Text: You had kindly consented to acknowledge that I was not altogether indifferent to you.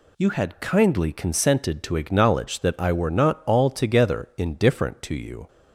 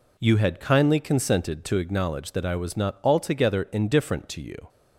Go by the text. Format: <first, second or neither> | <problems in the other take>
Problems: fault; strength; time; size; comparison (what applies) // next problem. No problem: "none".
second | says "were" for "was"; at 2.9 s